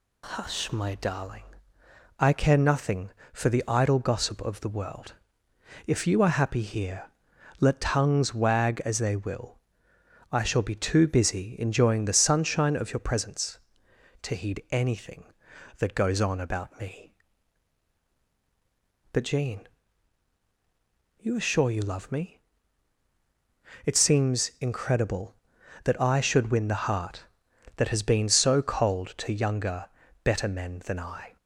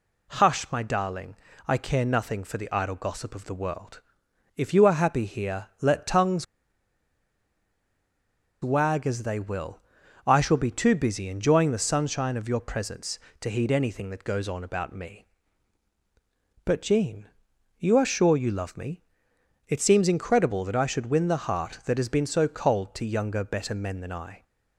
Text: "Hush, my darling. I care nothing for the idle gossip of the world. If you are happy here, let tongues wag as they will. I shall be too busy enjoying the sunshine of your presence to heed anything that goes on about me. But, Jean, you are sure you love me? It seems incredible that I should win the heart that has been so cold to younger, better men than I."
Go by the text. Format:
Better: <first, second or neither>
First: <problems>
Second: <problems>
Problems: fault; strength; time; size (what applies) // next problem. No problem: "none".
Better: first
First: none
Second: pauses between "tongues" and "wag"; strong; at 6.4 s; 2.1 s long